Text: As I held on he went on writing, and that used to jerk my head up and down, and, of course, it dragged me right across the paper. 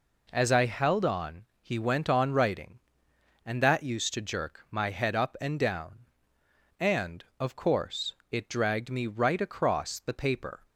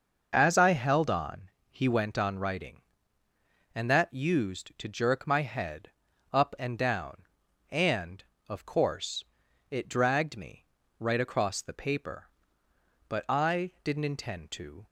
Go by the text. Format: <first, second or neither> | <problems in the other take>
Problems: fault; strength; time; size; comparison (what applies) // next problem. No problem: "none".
first | starts louder than the rest; noticeable; until 1.3 s; 6 dB // pauses between "on" and "he"; slight; at 1.4 s; 0.22 s long; slight in the first // pauses between "head" and "up"; at 5.9 s; 0.40 s long // pauses between "me" and "right"; slight; at 10.6 s; 0.32 s long // goes on to say "But I didn't intend to"; strong; from 13.0 s on; 1.7 s long